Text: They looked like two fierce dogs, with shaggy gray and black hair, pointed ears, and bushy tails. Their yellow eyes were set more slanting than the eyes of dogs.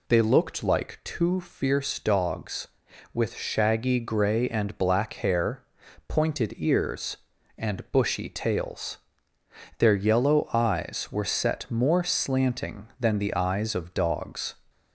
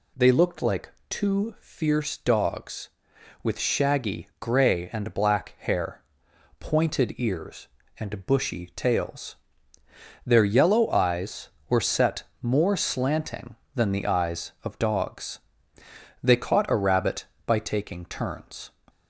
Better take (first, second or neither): first